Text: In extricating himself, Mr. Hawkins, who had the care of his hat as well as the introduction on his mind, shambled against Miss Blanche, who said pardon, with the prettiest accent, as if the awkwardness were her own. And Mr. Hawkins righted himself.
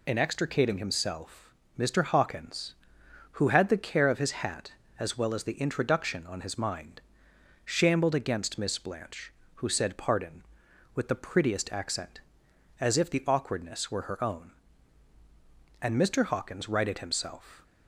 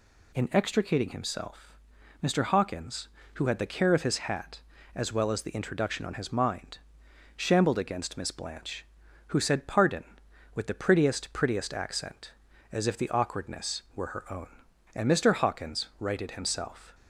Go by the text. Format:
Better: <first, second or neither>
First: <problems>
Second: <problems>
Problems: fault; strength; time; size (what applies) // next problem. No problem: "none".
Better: first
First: none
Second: says "prettiest" twice; at 11.3 s